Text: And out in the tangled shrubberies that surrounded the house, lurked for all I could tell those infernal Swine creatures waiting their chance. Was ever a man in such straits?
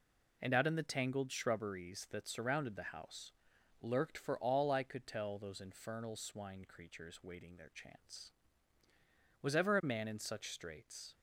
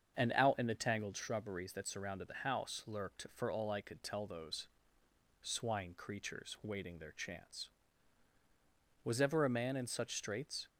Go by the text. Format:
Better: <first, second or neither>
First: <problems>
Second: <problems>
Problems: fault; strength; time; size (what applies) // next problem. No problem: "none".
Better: first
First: none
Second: starts louder than the rest; until 1.2 s; 7 dB // skips "infernal"; at 5.0 s